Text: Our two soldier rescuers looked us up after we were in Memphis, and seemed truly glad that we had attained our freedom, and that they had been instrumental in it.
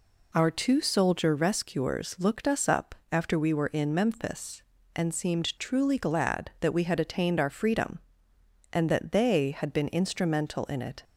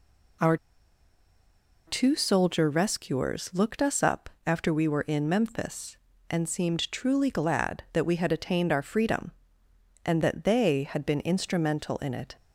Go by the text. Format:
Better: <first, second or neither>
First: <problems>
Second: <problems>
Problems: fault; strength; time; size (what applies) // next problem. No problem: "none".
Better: first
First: pauses between "up" and "after"; slight; at 2.9 s; 0.18 s long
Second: pauses between "Our" and "two"; strong; at 0.5 s; 1.2 s long // pauses between "up" and "after"; slight; at 4.2 s; 0.18 s long